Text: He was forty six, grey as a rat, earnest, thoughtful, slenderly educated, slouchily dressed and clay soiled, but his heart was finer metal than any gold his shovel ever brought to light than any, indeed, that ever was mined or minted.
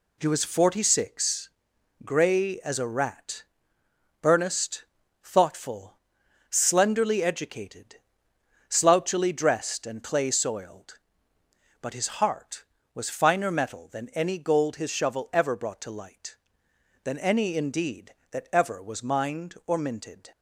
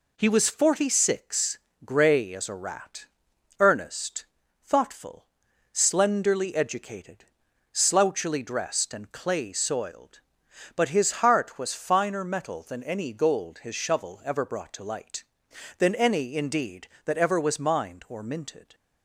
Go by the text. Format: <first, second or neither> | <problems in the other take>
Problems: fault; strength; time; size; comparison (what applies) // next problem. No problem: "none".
neither | none